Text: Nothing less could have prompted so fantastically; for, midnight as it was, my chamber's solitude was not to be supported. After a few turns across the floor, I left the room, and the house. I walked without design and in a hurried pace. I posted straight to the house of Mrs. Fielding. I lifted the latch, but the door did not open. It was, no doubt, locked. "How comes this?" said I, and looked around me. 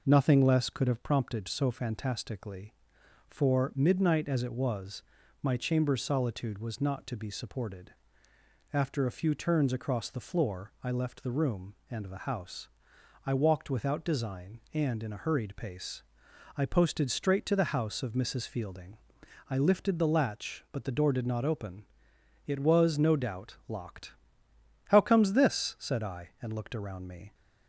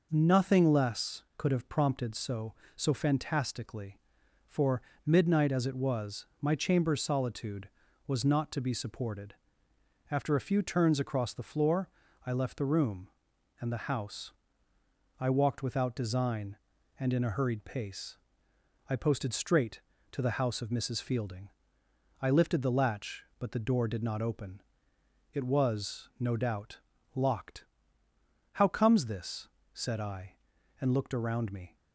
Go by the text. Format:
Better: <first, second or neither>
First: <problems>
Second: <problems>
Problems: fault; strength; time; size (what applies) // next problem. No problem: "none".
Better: first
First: none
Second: says "so" twice; at 2.7 s